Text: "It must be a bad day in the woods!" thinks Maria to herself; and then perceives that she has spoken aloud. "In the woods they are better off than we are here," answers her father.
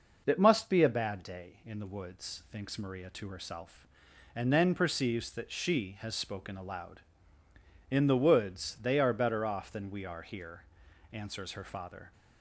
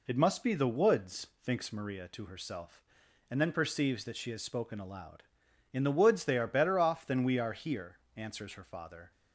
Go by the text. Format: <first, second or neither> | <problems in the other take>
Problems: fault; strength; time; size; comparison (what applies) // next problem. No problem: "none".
first | skips "a bad day in"; at 0.5 s